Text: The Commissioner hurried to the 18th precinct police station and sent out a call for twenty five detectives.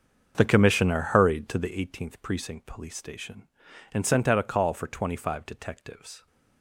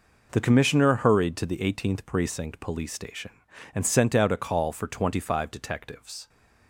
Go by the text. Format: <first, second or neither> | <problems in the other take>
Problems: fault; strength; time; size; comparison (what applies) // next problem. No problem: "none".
second | starts louder than the rest; until 1.8 s; 6.5 dB